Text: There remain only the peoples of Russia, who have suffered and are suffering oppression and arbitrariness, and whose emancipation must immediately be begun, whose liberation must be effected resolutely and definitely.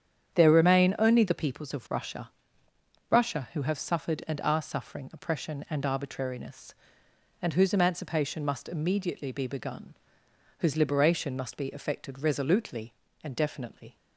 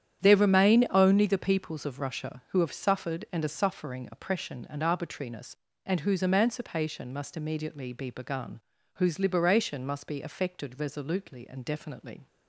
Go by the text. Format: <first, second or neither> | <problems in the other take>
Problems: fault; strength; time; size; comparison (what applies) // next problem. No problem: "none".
second | starts louder than the rest; strong; until 1.3 s; 8.5 dB; strong in the second // says "Russia" twice; at 3.0 s